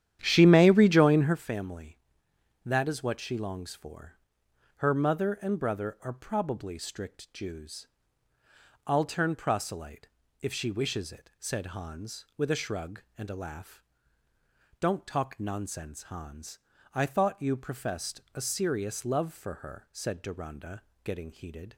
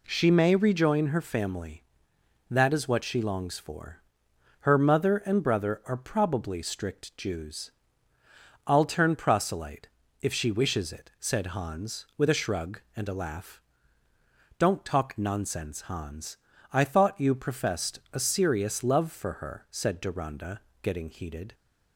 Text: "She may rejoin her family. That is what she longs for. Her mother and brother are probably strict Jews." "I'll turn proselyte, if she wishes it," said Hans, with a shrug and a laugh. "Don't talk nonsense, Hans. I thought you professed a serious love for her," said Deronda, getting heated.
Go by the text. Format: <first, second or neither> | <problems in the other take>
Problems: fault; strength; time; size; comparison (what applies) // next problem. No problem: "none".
second | starts louder than the rest; strong; until 1.4 s; 10.5 dB